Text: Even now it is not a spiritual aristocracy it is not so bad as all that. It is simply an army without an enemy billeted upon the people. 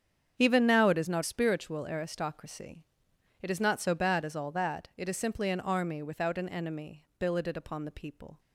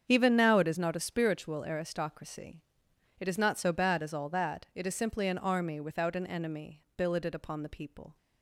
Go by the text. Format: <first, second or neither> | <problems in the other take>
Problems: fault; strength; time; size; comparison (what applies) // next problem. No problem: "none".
second | starts louder than the rest; strong; until 1.3 s; 8 dB; strong in the second // skips "a"; at 1.2 s // pauses between "aristocracy" and "it"; noticeable; at 2.8 s; 0.56 s long; noticeable in the second // pauses between "enemy" and "billeted"; slight; at 7.0 s; 0.16 s long; slight in the second